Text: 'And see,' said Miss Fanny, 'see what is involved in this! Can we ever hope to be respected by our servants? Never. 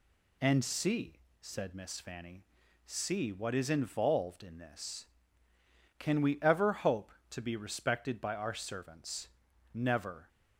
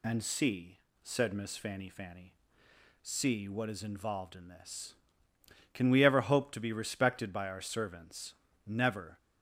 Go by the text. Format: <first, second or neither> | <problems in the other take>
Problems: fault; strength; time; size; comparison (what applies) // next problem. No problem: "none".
first | says "Fanny" twice; at 1.8 s